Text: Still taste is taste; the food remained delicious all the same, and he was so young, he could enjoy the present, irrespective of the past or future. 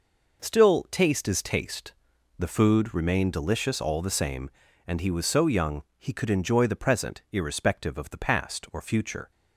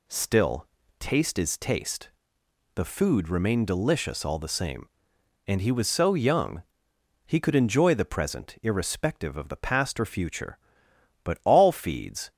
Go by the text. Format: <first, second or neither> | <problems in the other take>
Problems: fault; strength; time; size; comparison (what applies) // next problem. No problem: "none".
first | pauses between "Still" and "taste"; slight; at 0.6 s; 0.32 s long // goes on to say "But all feeds"; noticeable; from 11.2 s on; 1.0 s long